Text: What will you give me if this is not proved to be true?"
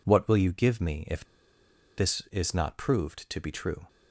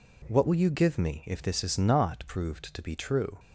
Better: second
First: pauses between "if" and "this"; noticeable; at 1.2 s; 0.74 s long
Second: none

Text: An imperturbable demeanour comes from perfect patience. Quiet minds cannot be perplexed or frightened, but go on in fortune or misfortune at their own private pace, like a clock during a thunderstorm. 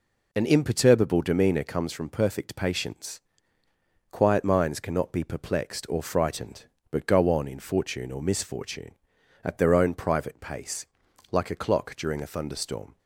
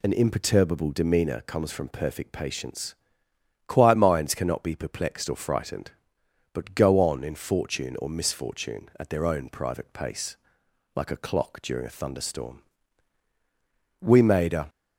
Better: first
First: none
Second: goes on to say "We made a"; noticeable; from 13.9 s on; 0.70 s long

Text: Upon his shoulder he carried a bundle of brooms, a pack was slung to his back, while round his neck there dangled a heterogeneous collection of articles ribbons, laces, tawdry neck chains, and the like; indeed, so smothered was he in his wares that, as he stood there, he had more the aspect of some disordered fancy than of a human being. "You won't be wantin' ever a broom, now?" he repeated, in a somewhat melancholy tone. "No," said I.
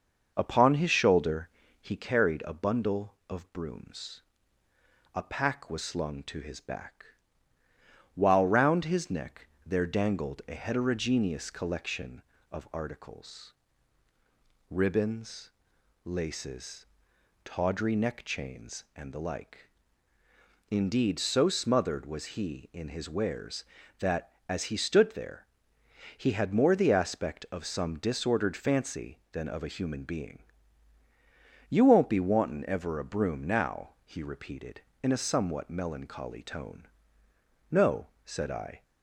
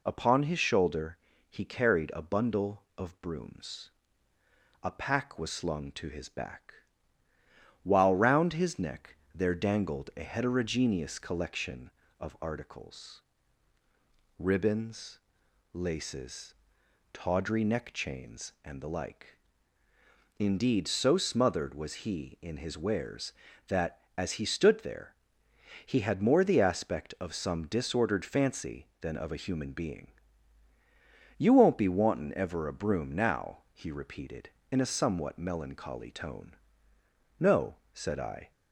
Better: second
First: starts louder than the rest; noticeable; until 2.1 s; 6 dB // pauses between "shoulder" and "he"; slight; at 1.4 s; 0.32 s long // pauses between "neck" and "there"; slight; at 9.4 s; 0.20 s long // pauses between "articles" and "ribbons"; at 13.5 s; 1.1 s long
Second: pauses between "shoulder" and "he"; slight; at 1.1 s; 0.32 s long // pauses between "neck" and "there"; slight; at 9.1 s; 0.20 s long // pauses between "articles" and "ribbons"; at 13.2 s; 1.1 s long

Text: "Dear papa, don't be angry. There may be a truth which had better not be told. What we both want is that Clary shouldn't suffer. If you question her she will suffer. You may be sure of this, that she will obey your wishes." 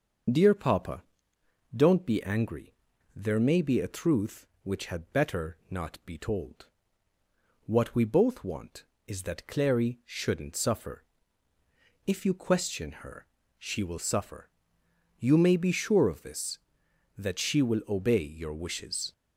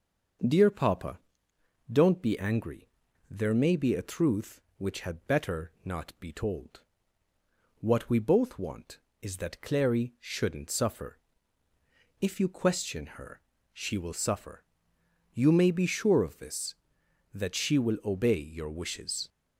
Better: second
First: loses the start of "Dear"; at 0.2 s; 25 ms // starts louder than the rest; until 2.0 s; 6 dB // pauses between "her" and "she"; slight; at 13.2 s; 0.32 s long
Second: starts louder than the rest; until 2.2 s; 6 dB // pauses between "her" and "she"; slight; at 13.4 s; 0.32 s long

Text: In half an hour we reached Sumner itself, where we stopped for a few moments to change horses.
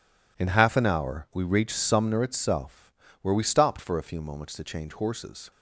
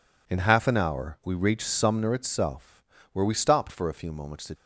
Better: first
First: none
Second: stops before "change horses"; at 4.5 s

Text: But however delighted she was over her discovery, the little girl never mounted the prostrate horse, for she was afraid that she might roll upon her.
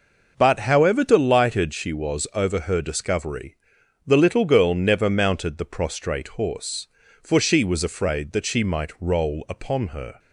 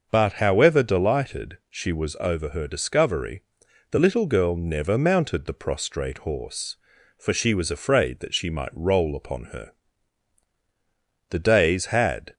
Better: first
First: none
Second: starts louder than the rest; noticeable; until 1.1 s; 6 dB // goes on to say "The days had"; noticeable; from 11.2 s on; 1.0 s long

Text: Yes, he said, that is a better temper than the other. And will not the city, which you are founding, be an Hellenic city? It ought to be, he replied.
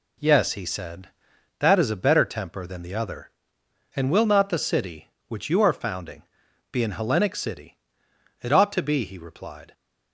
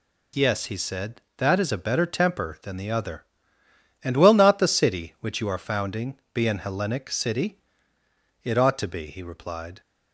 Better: neither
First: none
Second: none

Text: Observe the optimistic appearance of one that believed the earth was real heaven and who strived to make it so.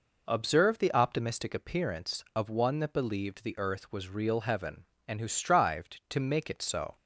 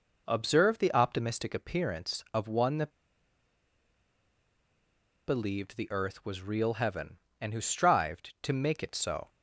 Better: first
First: none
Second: pauses between "that" and "believed"; strong; at 2.8 s; 2.3 s long

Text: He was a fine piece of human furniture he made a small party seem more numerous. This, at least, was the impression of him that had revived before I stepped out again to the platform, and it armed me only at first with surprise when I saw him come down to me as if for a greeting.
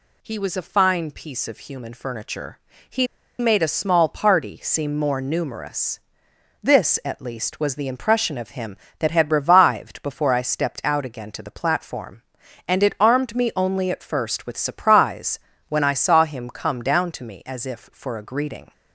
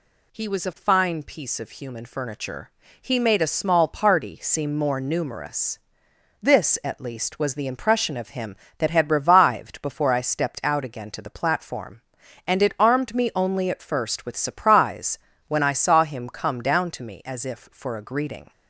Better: second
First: pauses between "furniture" and "he"; slight; at 2.5 s; 0.32 s long // pauses between "he" and "made"; slight; at 3.0 s; 0.34 s long // pauses between "surprise" and "when"; slight; at 15.3 s; 0.30 s long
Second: pauses between "furniture" and "he"; slight; at 2.6 s; 0.32 s long // pauses between "surprise" and "when"; slight; at 15.1 s; 0.30 s long

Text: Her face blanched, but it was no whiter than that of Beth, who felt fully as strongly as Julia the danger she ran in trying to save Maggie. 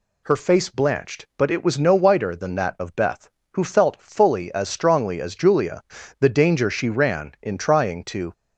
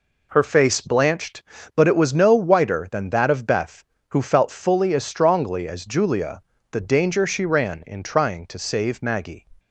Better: second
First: pauses between "Julia" and "the"; at 5.8 s; 0.38 s long // stops before "save Maggie"; at 8.3 s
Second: pauses between "Julia" and "the"; slight; at 6.4 s; 0.30 s long

